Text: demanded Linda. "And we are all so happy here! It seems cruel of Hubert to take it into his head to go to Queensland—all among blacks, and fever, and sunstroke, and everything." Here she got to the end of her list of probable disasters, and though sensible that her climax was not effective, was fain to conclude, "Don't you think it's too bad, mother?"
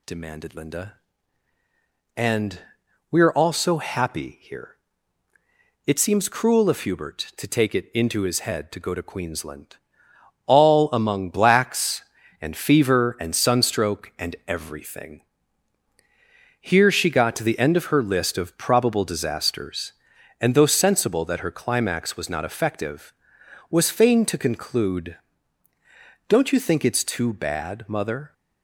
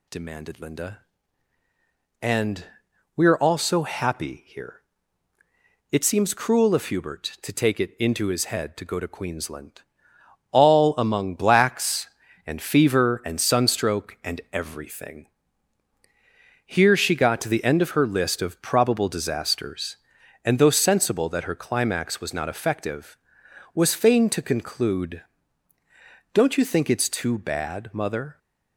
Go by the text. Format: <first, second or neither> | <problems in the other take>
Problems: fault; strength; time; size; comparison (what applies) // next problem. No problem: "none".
neither | pauses between "And" and "we"; noticeable; the same in both